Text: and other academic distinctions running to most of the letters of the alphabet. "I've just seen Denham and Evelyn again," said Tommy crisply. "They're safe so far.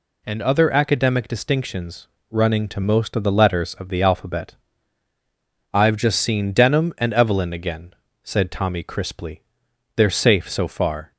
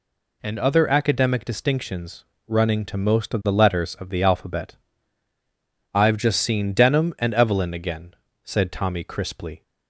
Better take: first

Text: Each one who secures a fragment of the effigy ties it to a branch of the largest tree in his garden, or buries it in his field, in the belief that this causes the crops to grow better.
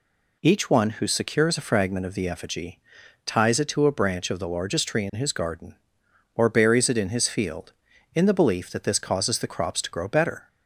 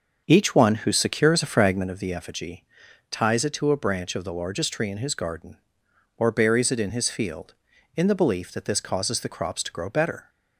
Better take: first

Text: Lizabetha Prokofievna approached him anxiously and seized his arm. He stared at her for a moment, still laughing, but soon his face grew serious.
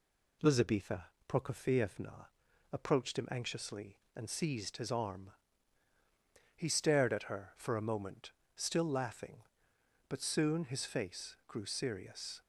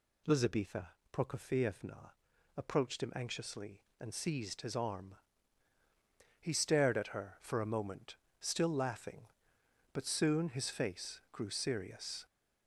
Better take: first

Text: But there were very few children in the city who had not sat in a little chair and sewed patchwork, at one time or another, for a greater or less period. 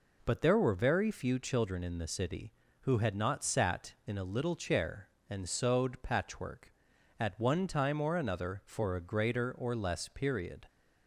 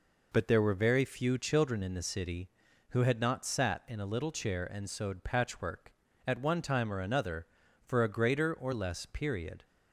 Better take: neither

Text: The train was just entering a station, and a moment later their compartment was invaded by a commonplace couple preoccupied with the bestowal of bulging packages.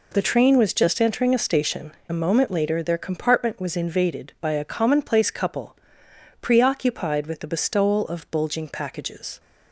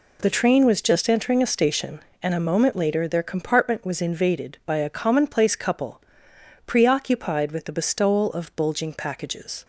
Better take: second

